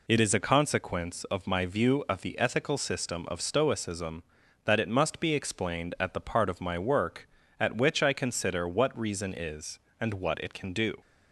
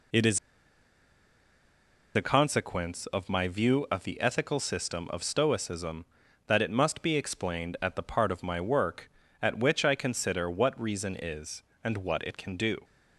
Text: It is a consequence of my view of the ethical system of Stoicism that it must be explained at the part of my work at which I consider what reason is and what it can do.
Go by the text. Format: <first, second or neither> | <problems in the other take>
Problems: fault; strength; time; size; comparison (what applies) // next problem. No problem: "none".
first | pauses between "is" and "a"; strong; at 0.3 s; 1.7 s long